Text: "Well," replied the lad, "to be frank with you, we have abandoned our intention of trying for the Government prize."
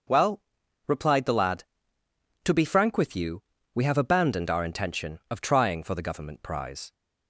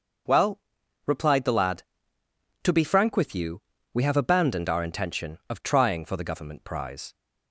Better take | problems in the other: neither | starts louder than the rest; the same in both

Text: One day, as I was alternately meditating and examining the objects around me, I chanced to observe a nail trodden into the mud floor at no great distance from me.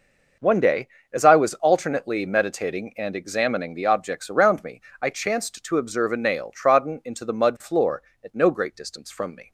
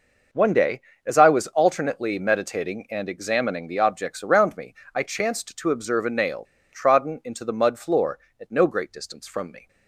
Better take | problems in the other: first | pauses between "nail" and "trodden"; slight; at 6.4 s; 0.28 s long

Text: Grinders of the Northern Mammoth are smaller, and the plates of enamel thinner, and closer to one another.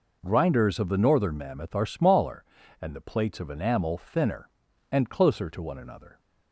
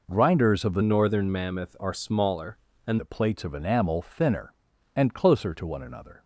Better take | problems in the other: first | changes voice from "Northern" to "and"; from 0.8 to 2.9 s; 2.1 s long

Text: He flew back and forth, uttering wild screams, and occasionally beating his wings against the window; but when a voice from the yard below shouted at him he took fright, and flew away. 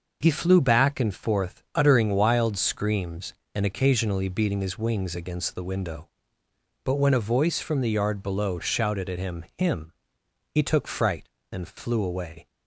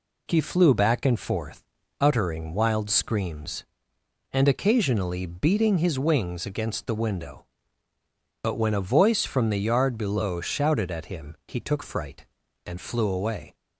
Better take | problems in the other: second | says "him" twice; at 9.5 s

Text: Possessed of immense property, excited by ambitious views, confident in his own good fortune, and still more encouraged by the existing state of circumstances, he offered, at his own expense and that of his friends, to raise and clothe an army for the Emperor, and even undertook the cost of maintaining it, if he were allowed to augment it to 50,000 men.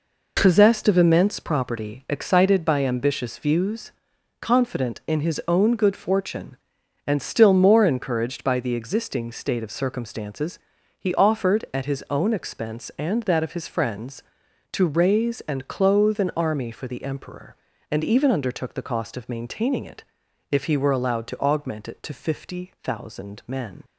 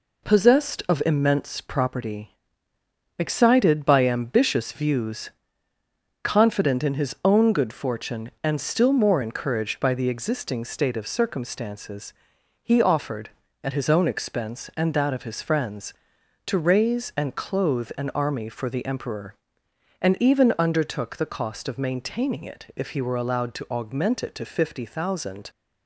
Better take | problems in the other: first | stops before "men"; at 25.4 s

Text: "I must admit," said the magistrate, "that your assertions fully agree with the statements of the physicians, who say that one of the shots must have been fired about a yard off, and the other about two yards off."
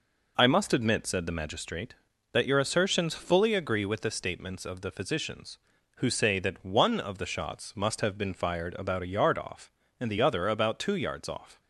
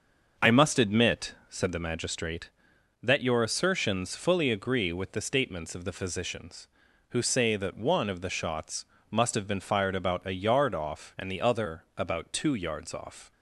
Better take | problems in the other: first | starts louder than the rest; until 1.7 s; 6.5 dB // pauses between "shots" and "must"; slight; at 8.8 s; 0.24 s long

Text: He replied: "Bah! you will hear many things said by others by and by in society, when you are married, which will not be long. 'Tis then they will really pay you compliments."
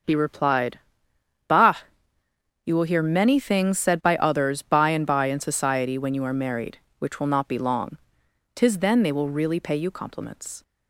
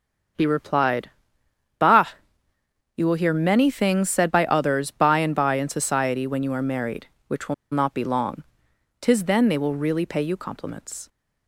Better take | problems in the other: first | starts louder than the rest; until 2.0 s; 6.5 dB; also in the first // pauses between "will" and "not"; slight; at 7.5 s; 0.17 s long

